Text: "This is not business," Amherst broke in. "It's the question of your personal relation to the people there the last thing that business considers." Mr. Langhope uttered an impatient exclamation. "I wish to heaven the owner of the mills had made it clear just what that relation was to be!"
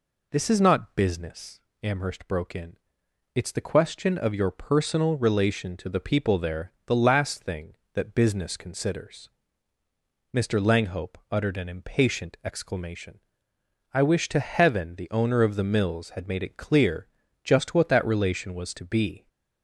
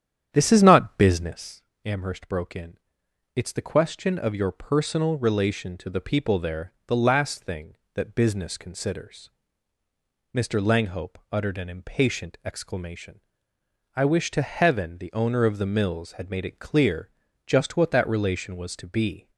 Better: first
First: pauses between "Langhope" and "uttered"; slight; at 11.1 s; 0.16 s long // pauses between "clear" and "just"; at 17.0 s; 0.38 s long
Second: starts louder than the rest; strong; until 1.6 s; 9.5 dB // pauses between "Langhope" and "uttered"; slight; at 11.1 s; 0.16 s long // pauses between "clear" and "just"; at 17.0 s; 0.38 s long

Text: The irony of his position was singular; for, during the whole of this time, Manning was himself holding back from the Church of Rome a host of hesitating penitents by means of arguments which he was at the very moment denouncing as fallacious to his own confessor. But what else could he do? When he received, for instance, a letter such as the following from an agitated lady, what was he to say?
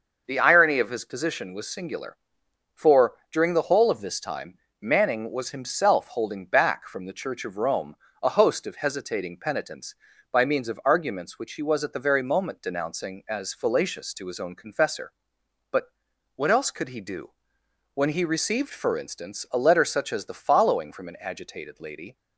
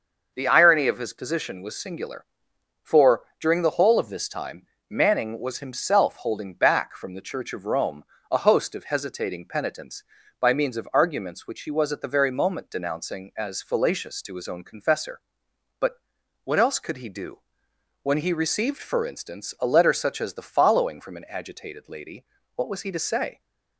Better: second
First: starts louder than the rest; until 1.2 s; 6 dB // pauses between "Rome" and "a"; slight; at 7.9 s; 0.30 s long // pauses between "But" and "what"; at 15.9 s; 0.42 s long // stops before "what was he to say"; at 22.1 s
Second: starts louder than the rest; until 1.3 s; 6 dB // pauses between "Rome" and "a"; slight; at 8.0 s; 0.30 s long // pauses between "But" and "what"; at 16.0 s; 0.42 s long

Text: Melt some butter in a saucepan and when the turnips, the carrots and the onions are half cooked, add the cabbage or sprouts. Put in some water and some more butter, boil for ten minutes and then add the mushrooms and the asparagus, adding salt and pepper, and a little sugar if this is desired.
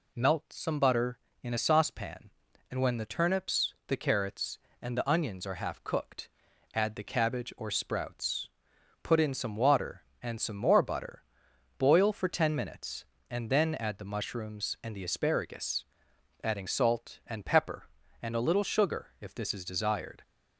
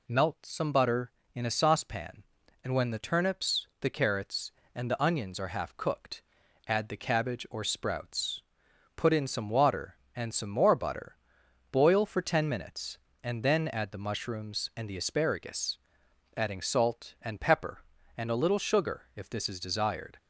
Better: neither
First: none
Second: none

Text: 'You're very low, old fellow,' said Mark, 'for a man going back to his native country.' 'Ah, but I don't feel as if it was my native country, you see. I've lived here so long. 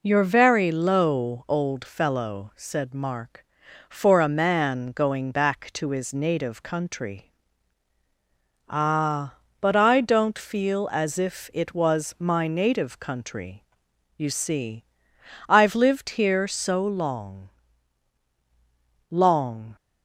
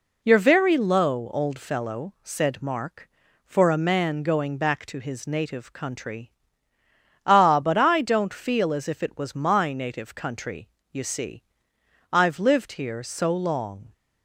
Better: second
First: says "long" twice; at 19.1 s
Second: none

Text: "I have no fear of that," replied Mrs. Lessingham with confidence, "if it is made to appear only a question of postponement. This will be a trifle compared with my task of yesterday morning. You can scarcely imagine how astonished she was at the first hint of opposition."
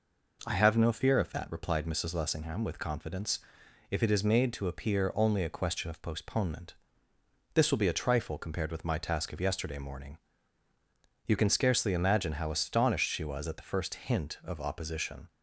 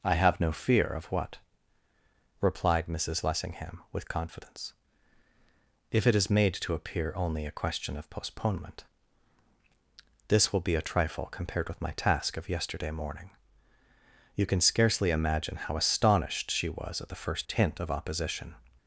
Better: first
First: none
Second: says "what" for "that"; at 1.0 s

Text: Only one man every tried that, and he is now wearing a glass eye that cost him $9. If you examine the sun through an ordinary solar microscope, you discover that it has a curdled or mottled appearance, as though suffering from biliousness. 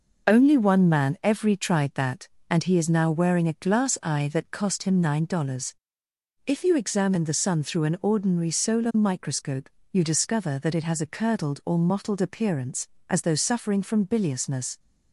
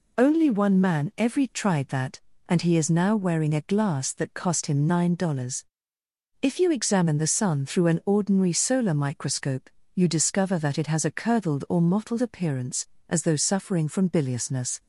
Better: first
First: none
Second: skips "eye"; at 4.1 s

